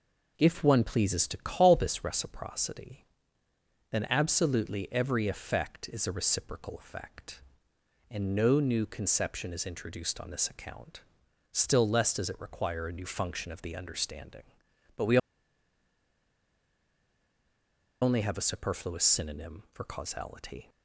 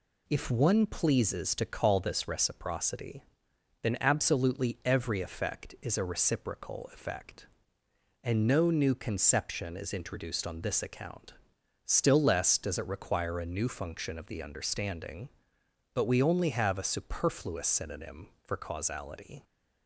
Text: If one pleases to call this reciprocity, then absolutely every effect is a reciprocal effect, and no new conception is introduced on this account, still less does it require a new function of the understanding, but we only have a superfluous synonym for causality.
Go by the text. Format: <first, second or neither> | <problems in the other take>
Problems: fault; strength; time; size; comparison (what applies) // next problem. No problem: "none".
second | pauses between "we" and "only"; strong; at 15.1 s; 2.8 s long